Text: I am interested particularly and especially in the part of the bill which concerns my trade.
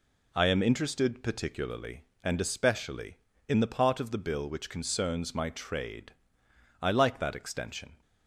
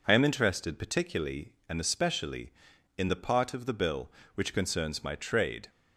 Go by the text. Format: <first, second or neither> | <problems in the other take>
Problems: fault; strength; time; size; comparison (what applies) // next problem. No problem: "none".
second | goes on to say "I like that extension"; noticeable; from 6.8 s on; 1.2 s long